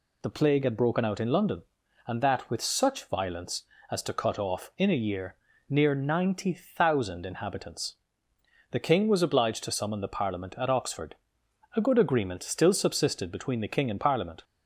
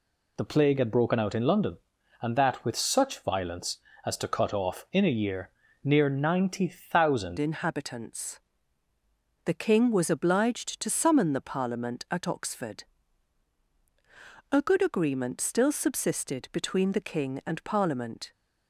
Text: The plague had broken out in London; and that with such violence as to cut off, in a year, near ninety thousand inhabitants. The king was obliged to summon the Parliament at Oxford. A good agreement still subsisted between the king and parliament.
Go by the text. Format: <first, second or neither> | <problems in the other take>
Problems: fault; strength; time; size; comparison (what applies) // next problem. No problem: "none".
first | changes voice at "inhabitants"; from 7.3 s on; 11.0 s long